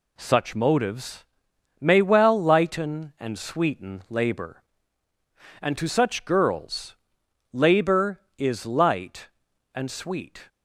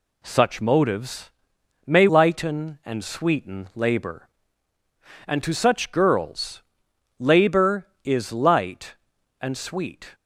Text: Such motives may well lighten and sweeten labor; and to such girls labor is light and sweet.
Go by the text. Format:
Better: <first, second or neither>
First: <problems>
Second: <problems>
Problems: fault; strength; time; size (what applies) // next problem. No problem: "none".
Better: first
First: pauses between "motives" and "may"; noticeable; at 1.2 s; 0.54 s long // pauses between "girls" and "labor"; noticeable; at 6.9 s; 0.56 s long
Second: pauses between "motives" and "may"; noticeable; at 1.3 s; 0.54 s long // skips "well"; at 2.0 s // pauses between "girls" and "labor"; noticeable; at 6.6 s; 0.56 s long